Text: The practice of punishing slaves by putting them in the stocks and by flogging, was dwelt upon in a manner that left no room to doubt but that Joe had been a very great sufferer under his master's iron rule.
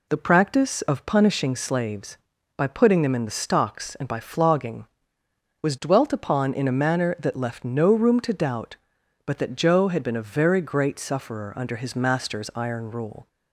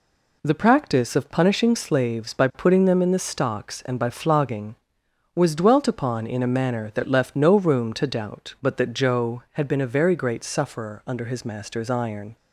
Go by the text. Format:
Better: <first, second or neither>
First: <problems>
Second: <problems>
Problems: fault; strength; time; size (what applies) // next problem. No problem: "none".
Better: first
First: none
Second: stops before "rule"; at 12.3 s